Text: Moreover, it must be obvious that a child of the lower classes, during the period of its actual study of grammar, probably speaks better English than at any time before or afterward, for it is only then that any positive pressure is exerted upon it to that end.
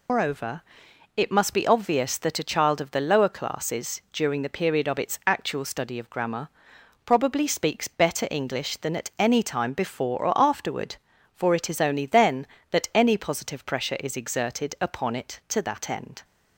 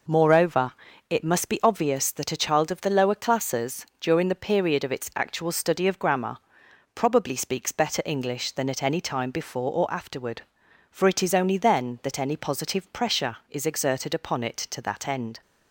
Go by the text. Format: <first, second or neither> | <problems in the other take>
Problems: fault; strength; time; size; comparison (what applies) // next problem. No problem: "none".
second | loses the start of "Moreover"; at 0.0 s; 140 ms